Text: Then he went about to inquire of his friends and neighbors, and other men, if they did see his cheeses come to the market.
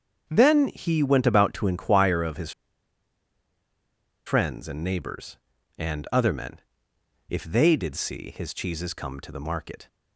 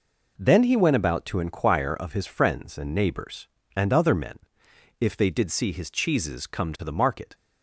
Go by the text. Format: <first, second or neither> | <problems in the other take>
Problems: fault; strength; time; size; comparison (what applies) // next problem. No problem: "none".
second | starts louder than the rest; until 1.2 s; 7 dB // pauses between "his" and "friends"; strong; at 2.5 s; 1.7 s long